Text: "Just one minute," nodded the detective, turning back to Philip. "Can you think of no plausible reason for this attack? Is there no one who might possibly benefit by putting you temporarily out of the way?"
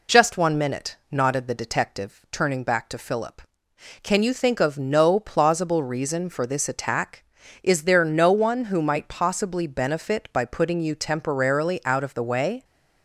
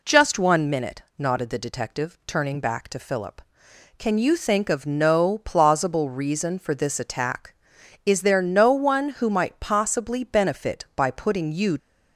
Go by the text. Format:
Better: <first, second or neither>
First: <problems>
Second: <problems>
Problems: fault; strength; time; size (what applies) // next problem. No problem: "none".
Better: first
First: none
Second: stops before "temporarily out of the way"; at 11.7 s